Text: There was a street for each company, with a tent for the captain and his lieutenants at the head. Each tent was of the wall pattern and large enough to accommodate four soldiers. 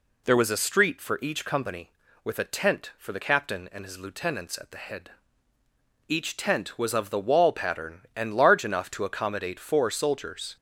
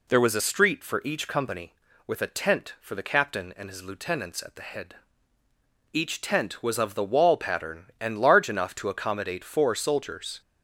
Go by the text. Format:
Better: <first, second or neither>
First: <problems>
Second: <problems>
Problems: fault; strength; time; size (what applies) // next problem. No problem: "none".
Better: neither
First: none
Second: none